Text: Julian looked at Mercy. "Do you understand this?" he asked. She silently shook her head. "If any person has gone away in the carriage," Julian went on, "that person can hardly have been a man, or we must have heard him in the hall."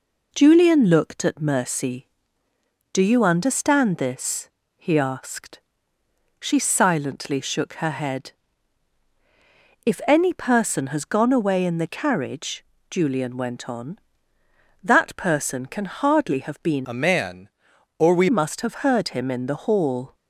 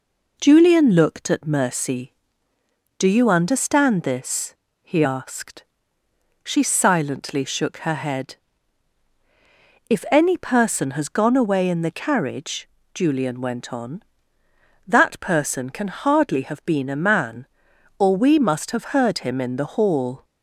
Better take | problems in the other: second | changes voice from "a" to "we"; from 16.8 to 18.2 s; 1.4 s long

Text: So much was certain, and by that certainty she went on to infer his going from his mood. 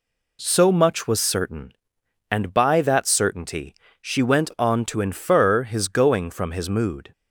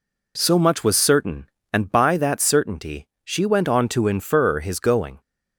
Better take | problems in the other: first | pauses between "certainty" and "she"; slight; at 3.0 s; 0.18 s long; slight in the first // stops before "from his mood"; at 5.2 s

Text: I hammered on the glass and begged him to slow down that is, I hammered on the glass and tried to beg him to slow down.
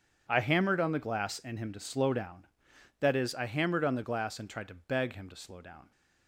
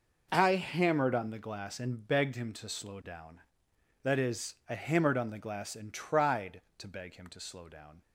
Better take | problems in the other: second | starts louder than the rest; strong; until 1.3 s; 8 dB // skips "begged"; at 1.5 s

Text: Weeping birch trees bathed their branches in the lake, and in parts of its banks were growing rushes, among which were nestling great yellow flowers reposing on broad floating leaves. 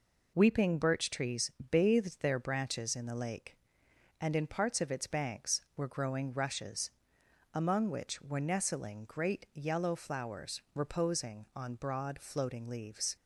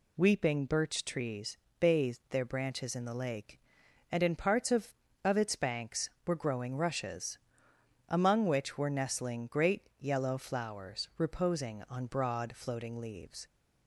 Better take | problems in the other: first | pauses between "trees" and "bathed"; slight; at 1.5 s; 0.24 s long; slight in the first // says "of" twice; at 5.2 s

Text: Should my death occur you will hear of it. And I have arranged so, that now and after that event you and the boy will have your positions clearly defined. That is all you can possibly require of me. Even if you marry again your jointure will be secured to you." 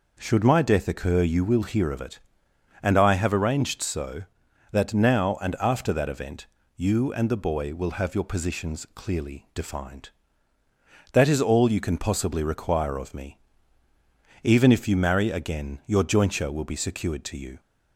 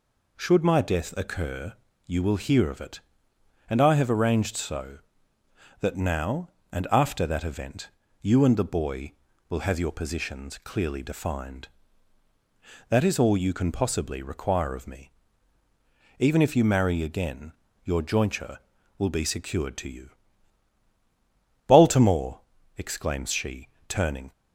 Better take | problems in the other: first | pauses between "occur" and "you"; slight; at 1.7 s; 0.34 s long // pauses between "event" and "you"; slight; at 7.9 s; 0.32 s long; slight in the first // pauses between "again" and "your"; slight; at 17.5 s; 0.32 s long // goes on to say "Baltimore exclaims she turning"; strong; from 21.6 s on; 2.6 s long

